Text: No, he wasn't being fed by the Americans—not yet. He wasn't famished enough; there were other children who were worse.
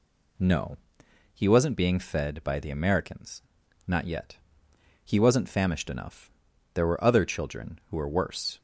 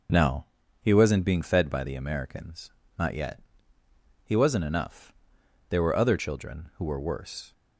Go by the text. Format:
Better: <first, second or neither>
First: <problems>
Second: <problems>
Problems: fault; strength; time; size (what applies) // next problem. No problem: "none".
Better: first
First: none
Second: skips "famished"; at 4.6 s